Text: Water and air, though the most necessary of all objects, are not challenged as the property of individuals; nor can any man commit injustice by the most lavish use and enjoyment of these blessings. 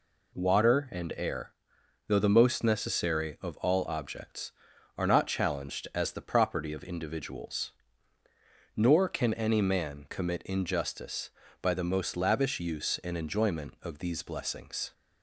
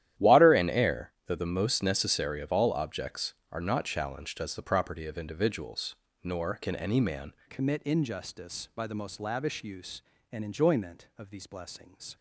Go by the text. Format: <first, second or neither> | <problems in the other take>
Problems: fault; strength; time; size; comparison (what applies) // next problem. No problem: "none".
first | starts louder than the rest; strong; until 1.3 s; 12 dB // changes voice at "commit"; from 7.4 s on; 4.7 s long